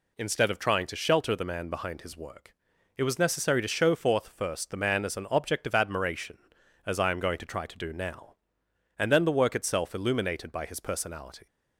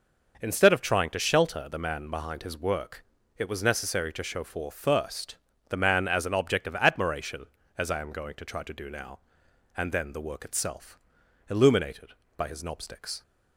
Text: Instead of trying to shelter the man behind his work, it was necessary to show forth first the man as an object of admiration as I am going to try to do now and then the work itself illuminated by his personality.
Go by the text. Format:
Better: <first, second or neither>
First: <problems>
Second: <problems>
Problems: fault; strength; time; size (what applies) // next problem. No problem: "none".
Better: first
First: none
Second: pauses between "first" and "the"; slight; at 5.3 s; 0.32 s long // pauses between "itself" and "illuminated"; noticeable; at 10.9 s; 0.52 s long // says "knobsticks" for "personality"; at 12.6 s